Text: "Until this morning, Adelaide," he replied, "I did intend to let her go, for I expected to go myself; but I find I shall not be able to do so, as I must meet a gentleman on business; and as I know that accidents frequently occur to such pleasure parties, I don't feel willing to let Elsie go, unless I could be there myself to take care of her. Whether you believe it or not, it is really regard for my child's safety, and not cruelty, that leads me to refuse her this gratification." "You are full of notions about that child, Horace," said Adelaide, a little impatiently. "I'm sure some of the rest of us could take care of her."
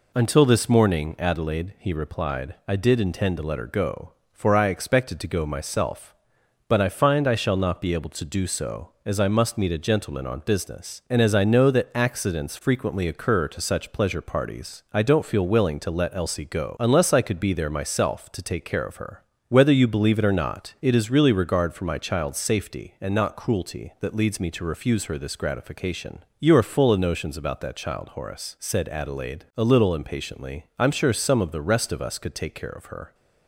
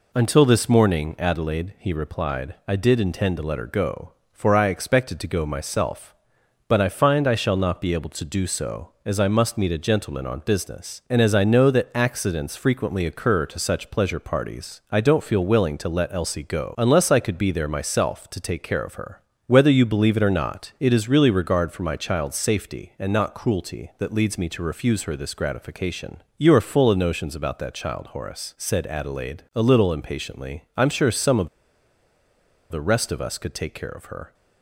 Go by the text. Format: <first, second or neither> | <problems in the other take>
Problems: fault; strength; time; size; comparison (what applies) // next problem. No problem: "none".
first | pauses between "of" and "the"; at 31.4 s; 1.2 s long